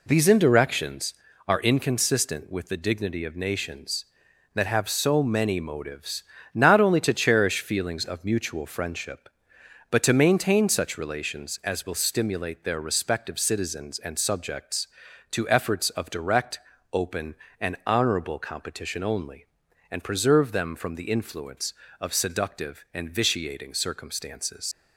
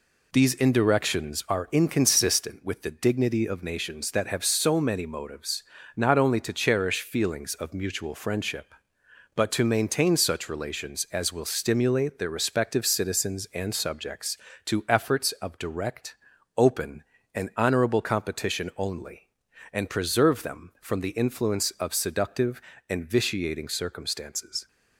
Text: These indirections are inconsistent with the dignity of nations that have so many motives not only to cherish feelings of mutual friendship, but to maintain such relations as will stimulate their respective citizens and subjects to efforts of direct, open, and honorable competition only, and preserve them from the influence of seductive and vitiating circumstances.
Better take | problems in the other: second | pauses between "motives" and "not"; slight; at 6.2 s; 0.30 s long; slight in the second // leaves "circumstances" unfinished; at 24.7 s; 85 ms

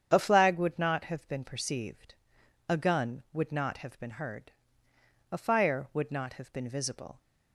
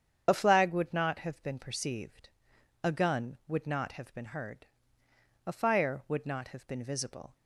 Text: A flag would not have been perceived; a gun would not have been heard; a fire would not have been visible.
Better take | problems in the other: first | loses the start of "A"; at 0.2 s; 25 ms // starts louder than the rest; strong; until 1.2 s; 8 dB; strong in the first

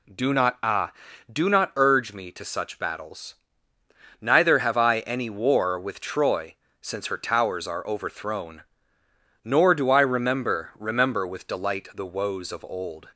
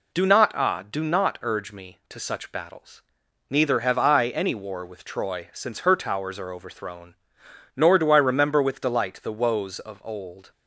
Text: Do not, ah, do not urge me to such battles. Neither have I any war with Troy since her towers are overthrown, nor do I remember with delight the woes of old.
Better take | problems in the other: second | pauses between "Troy" and "since"; slight; at 6.5 s; 0.26 s long // says "remember" twice; at 10.7 s

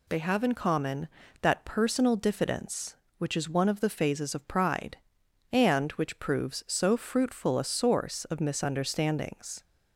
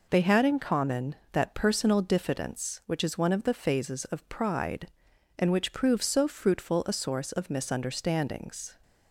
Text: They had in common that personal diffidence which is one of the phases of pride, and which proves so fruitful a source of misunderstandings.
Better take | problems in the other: second | says "have" for "had"; at 0.1 s

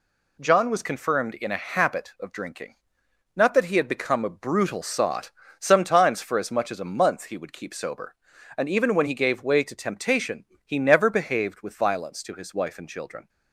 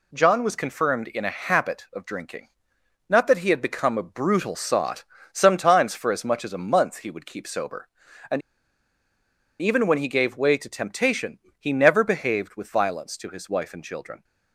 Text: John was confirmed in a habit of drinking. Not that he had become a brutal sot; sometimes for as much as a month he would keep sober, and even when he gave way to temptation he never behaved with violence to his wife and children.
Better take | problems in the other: first | pauses between "and" and "even"; at 8.4 s; 1.2 s long // pauses between "temptation" and "he"; slight; at 11.3 s; 0.22 s long; slight in the first

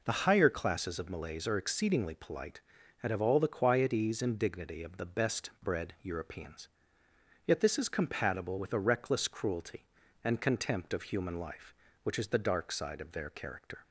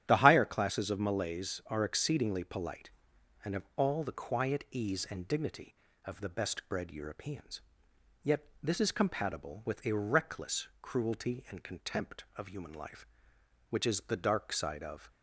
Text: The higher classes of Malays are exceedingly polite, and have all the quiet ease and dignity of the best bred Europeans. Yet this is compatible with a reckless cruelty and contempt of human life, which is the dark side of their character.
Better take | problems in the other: first | starts louder than the rest; strong; until 1.0 s; 11 dB // pauses between "Yet" and "this"; slight; at 8.4 s; 0.16 s long // stops before "their character"; at 15.1 s

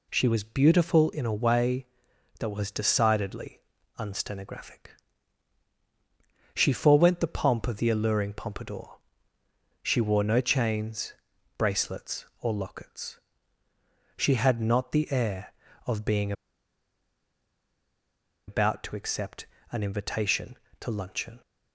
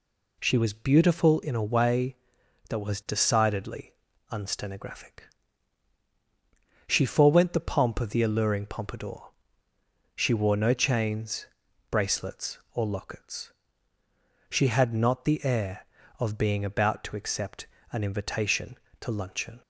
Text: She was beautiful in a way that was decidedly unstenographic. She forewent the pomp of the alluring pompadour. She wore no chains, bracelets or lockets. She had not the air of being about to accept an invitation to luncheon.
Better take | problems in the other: second | pauses between "decidedly" and "unstenographic"; at 3.6 s; 0.38 s long; also in the second // pauses between "being" and "about"; strong; at 16.3 s; 2.1 s long // pauses between "accept" and "an"; slight; at 19.4 s; 0.26 s long; slight in the second

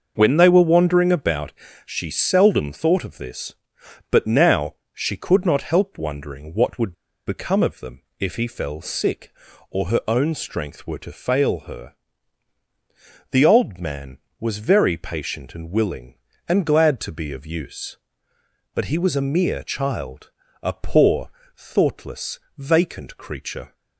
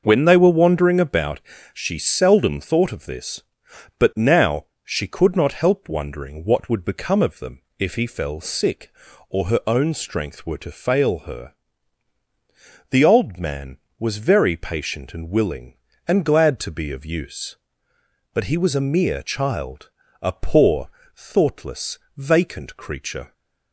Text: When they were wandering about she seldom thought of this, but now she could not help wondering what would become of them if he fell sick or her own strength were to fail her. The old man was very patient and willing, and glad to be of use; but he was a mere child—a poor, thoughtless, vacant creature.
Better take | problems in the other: second | pauses between "about" and "she"; slight; at 1.5 s; 0.32 s long; slight in the second // pauses between "now" and "she"; slight; at 4.7 s; 0.18 s long; slight in the second // pauses between "would" and "become"; slight; at 6.9 s; 0.32 s long // pauses between "them" and "if"; slight; at 8.0 s; 0.16 s long; slight in the second

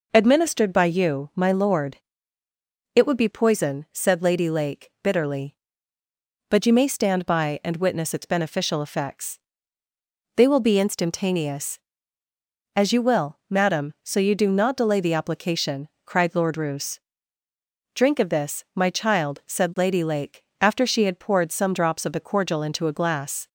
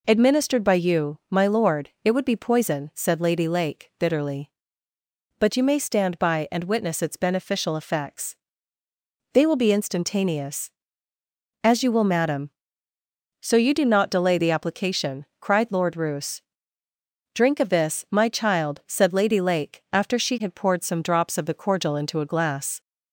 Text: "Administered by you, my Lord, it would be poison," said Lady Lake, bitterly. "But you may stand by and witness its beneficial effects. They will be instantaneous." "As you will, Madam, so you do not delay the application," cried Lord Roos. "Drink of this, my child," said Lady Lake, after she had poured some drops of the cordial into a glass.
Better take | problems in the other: neither | none

